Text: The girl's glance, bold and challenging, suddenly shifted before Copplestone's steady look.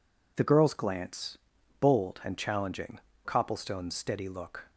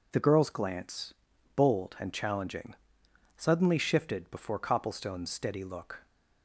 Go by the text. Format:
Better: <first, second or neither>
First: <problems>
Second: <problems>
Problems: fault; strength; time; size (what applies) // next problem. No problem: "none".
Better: second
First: skips "suddenly shifted before"; at 3.1 s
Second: none